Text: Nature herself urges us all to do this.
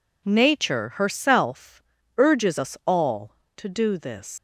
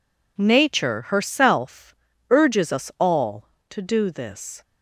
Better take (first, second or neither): second